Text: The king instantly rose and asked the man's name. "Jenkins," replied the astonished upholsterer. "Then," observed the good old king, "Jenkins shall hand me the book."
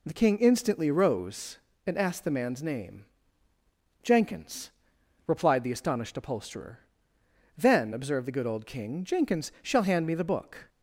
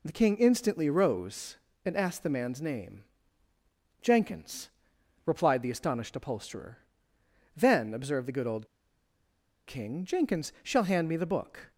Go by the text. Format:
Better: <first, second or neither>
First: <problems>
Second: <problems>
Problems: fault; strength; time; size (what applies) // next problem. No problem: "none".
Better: first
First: none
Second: pauses between "old" and "king"; at 8.6 s; 1.0 s long